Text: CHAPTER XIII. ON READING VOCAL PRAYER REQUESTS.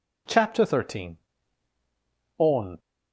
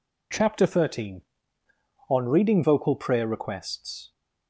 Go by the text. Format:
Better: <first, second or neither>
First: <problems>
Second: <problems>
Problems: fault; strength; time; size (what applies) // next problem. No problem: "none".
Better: second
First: stops before "READING VOCAL PRAYER REQUESTS"; at 2.7 s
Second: none